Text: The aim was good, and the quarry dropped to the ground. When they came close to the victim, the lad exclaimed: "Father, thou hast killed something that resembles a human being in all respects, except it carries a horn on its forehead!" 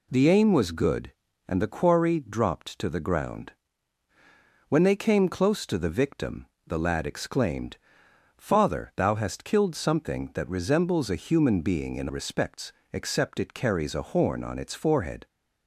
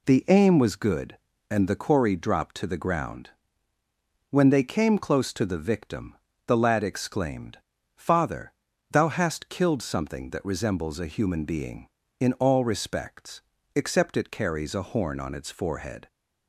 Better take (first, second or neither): second